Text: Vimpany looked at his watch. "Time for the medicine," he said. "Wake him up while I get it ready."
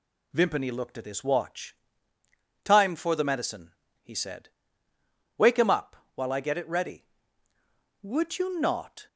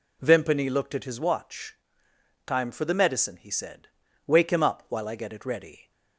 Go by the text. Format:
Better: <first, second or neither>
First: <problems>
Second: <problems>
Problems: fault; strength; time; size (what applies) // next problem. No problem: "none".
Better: second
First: pauses between "up" and "while"; slight; at 5.9 s; 0.18 s long // goes on to say "Would you not"; noticeable; from 8.0 s on; 1.0 s long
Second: none